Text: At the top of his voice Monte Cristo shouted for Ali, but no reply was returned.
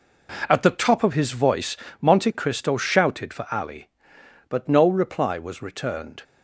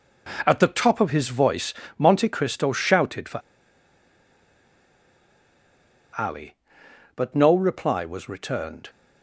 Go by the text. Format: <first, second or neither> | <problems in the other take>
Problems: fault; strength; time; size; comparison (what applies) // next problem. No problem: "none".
first | pauses between "voice" and "Monte"; slight; at 1.7 s; 0.24 s long; slight in the first // pauses between "for" and "Ali"; strong; at 3.3 s; 2.7 s long